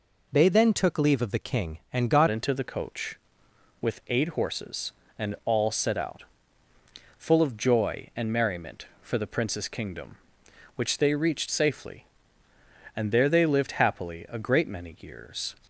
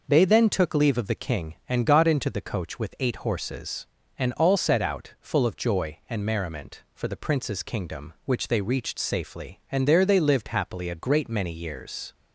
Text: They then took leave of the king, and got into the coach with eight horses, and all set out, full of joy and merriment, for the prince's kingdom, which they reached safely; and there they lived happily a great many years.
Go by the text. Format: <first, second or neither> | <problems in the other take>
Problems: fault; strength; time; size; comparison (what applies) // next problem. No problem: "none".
second | changes voice at "into"; from 2.2 s on; 13.3 s long